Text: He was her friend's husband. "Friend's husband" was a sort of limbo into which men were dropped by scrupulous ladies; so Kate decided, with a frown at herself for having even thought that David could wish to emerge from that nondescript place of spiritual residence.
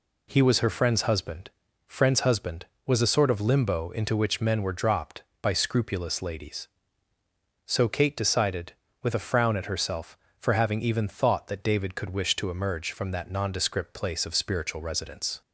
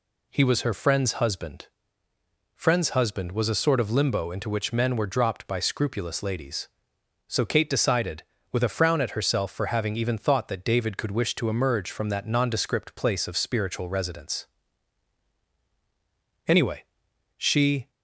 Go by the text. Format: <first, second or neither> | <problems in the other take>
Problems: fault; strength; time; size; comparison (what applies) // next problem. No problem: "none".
first | goes on to say "Anyway she"; from 16.4 s on; 1.4 s long